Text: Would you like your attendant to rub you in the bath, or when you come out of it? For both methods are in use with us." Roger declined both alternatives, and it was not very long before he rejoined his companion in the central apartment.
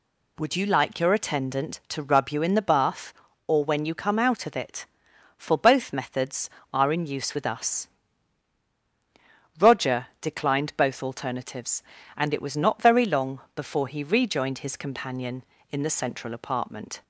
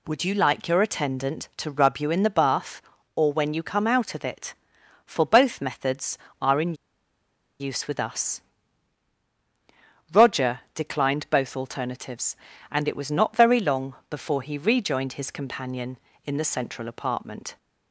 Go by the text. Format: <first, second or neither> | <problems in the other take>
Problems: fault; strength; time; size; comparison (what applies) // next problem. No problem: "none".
first | pauses between "in" and "use"; noticeable; at 6.7 s; 0.86 s long